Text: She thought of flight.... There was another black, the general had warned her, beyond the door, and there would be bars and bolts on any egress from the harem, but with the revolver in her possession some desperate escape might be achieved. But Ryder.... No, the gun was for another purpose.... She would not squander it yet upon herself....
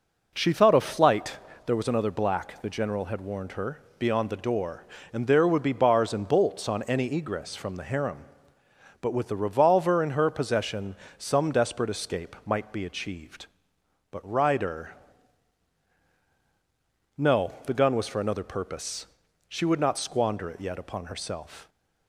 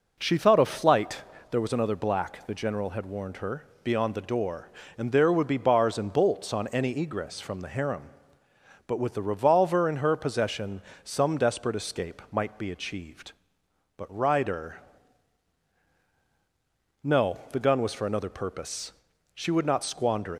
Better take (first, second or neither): first